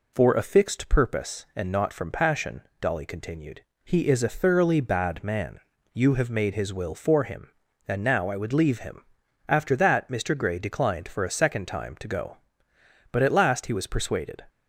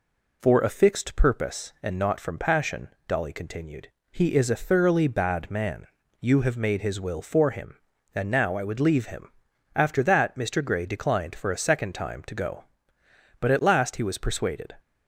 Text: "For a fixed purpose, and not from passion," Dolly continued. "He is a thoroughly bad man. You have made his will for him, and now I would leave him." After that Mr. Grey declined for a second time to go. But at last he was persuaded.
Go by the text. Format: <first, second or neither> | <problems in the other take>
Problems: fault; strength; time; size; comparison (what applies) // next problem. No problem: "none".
neither | none